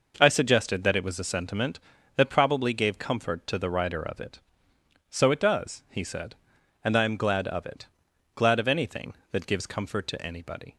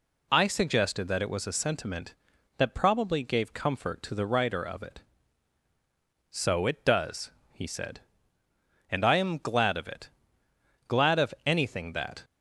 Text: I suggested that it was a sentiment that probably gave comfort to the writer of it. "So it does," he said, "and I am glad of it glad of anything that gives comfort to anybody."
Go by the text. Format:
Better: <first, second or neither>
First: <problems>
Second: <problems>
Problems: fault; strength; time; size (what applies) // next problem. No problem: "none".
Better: first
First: pauses between "it" and "glad"; noticeable; at 7.8 s; 0.48 s long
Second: pauses between "it" and "glad"; noticeable; at 10.1 s; 0.78 s long // stops before "gives comfort to anybody"; at 12.2 s